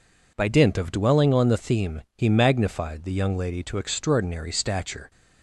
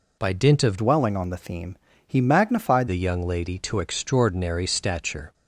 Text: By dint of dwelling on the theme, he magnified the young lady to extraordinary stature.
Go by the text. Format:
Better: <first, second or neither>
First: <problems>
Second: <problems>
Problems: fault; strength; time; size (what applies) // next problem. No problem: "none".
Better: first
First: none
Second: changes voice from "dwelling" to "magnified"; from 0.7 to 2.8 s; 2.1 s long